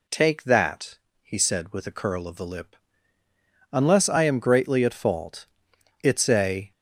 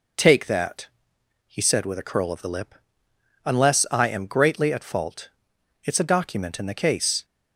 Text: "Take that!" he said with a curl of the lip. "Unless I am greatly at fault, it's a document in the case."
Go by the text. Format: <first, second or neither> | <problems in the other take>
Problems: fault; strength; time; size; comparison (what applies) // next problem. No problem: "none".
second | stops before "document in the case"; at 6.7 s